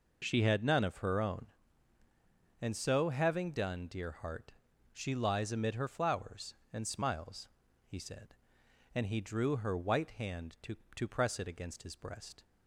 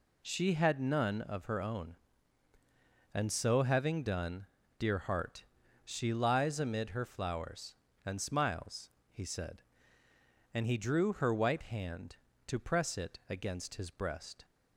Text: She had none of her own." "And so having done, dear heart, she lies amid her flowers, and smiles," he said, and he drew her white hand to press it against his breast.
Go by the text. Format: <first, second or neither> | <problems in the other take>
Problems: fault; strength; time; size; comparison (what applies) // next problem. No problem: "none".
second | says "to" twice; at 10.9 s